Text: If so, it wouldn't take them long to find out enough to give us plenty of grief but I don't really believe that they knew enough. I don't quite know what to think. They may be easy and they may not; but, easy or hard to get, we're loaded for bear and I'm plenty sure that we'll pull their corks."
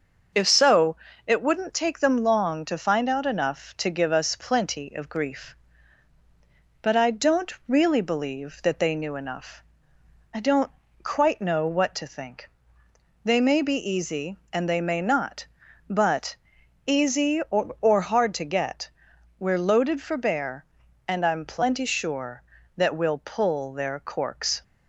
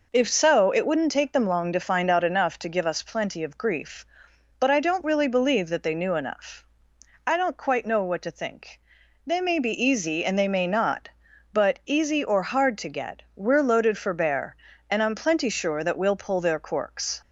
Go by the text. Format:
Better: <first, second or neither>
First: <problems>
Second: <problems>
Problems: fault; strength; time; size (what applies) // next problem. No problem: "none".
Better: second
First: starts louder than the rest; until 1.6 s; 6.5 dB // pauses between "don't" and "really"; slight; at 7.5 s; 0.16 s long // pauses between "don't" and "quite"; slight; at 10.7 s; 0.32 s long // says "or" twice; at 17.8 s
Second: none